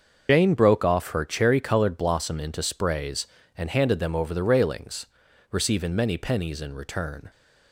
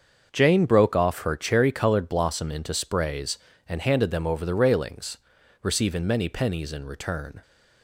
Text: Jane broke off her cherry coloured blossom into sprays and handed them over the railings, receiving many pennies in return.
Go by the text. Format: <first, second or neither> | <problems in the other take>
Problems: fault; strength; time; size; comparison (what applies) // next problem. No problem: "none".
second | loses the start of "Jane"; at 0.2 s; 95 ms // starts louder than the rest; until 1.3 s; 6.5 dB; also in the second